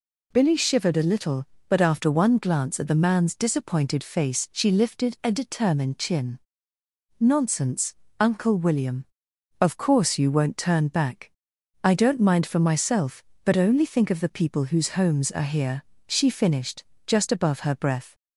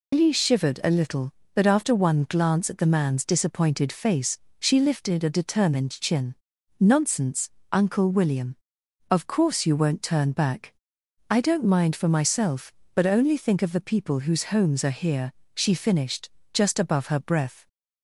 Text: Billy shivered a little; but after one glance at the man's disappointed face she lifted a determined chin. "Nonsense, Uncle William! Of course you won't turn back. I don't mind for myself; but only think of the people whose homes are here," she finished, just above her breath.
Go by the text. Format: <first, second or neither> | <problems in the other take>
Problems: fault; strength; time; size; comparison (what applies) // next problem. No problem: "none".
first | loses the start of "Billy"; at 0.1 s; 90 ms // pauses between "face" and "she"; slight; at 4.3 s; 0.20 s long